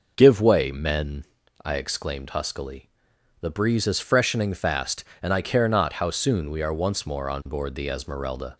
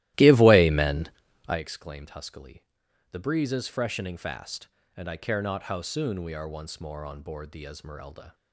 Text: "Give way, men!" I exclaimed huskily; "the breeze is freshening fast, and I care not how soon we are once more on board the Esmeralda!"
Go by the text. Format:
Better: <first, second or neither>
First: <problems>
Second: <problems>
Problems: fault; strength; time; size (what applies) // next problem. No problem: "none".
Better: first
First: none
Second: starts louder than the rest; strong; until 1.6 s; 16 dB